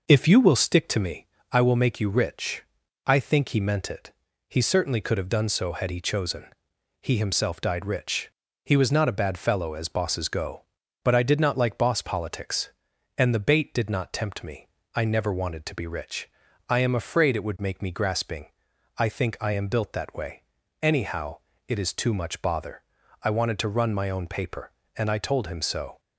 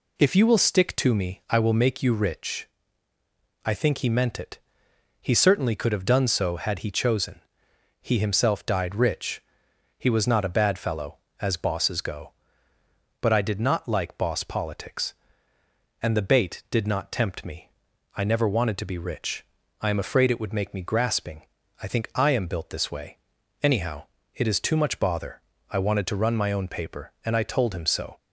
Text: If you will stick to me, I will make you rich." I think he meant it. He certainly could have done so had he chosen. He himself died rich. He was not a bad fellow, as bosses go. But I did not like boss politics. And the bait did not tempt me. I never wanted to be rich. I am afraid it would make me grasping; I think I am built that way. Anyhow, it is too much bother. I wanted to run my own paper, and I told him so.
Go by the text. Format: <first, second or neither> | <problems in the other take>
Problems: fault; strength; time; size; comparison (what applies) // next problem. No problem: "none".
first | says "this" for "that"; at 22.6 s